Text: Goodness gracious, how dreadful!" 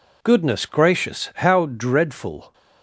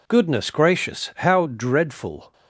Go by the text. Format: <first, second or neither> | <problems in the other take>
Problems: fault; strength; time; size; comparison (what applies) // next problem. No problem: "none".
neither | none